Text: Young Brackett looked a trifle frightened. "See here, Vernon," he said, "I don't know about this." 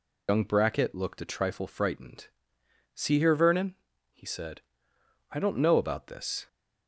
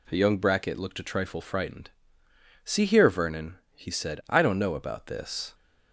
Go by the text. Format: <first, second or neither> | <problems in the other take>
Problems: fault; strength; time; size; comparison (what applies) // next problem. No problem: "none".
second | loses the start of "Young"; at 0.2 s; 95 ms